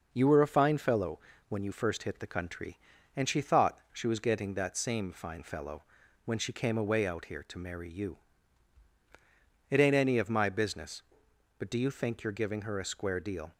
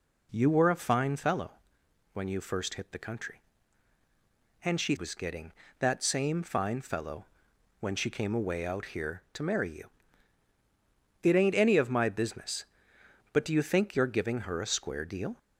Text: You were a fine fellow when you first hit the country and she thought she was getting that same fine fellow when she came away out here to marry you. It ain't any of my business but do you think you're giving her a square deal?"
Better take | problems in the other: first | pauses between "fellow" and "when"; noticeable; at 1.5 s; 0.62 s long; slight in the first // skips "thought she"; at 4.9 s // pauses between "fellow" and "when"; noticeable; at 7.2 s; 0.56 s long; also in the first

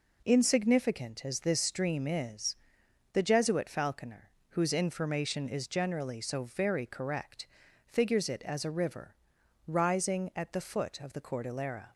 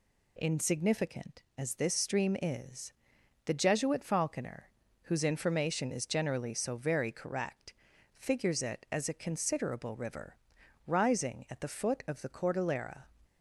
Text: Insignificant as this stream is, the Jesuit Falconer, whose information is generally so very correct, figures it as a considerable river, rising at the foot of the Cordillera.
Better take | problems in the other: second | skips "considerable"; at 8.7 s

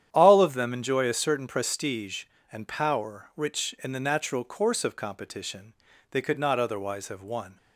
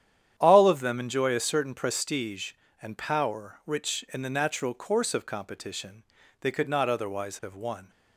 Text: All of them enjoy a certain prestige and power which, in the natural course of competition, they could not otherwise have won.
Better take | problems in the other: neither | starts louder than the rest; strong; the same in both

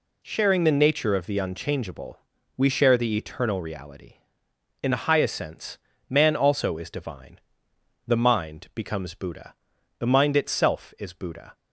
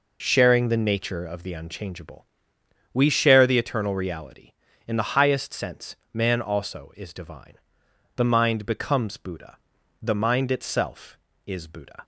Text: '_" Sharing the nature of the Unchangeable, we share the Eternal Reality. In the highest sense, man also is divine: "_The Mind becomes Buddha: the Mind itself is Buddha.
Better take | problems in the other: neither | none

